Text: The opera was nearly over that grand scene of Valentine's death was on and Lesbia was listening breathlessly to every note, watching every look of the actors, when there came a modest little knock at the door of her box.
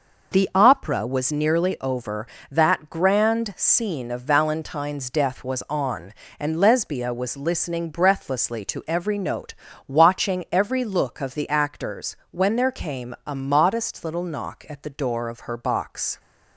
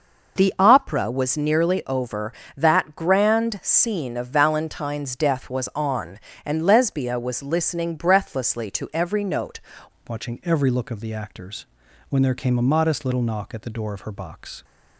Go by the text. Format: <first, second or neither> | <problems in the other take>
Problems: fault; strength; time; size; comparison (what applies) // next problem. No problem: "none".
first | changes voice at "watching"; from 10.0 s on; 4.6 s long